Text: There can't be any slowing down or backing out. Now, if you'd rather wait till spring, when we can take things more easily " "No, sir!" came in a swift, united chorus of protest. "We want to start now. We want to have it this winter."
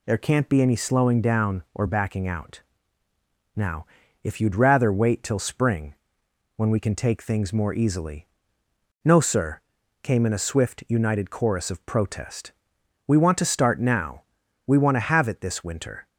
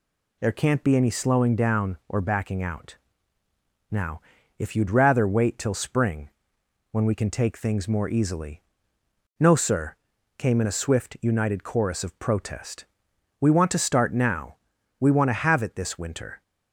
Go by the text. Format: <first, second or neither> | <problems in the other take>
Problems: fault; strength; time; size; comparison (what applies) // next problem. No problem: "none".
neither | none